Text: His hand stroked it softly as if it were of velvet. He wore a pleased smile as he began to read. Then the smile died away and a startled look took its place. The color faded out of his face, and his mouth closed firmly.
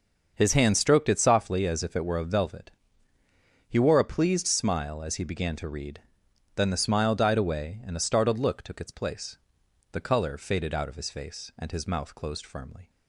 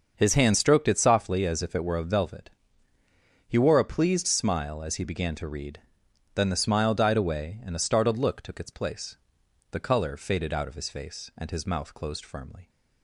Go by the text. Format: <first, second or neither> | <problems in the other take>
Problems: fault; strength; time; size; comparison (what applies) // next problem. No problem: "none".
neither | starts louder than the rest; the same in both